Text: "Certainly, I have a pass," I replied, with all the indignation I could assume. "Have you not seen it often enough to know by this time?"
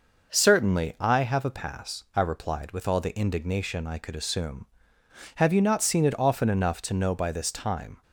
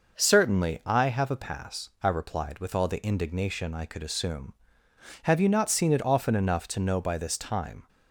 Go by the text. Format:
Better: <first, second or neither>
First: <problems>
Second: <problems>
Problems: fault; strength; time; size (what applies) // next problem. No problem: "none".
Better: neither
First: none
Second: none